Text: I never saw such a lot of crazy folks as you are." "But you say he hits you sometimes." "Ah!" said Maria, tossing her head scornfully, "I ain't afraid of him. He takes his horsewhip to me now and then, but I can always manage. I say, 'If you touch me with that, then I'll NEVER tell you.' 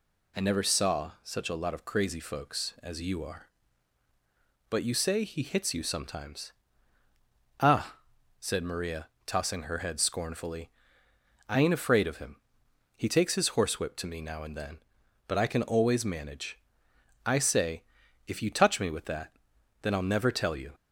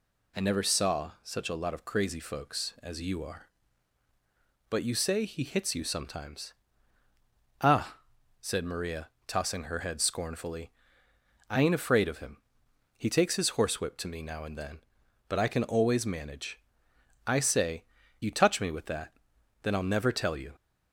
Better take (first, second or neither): first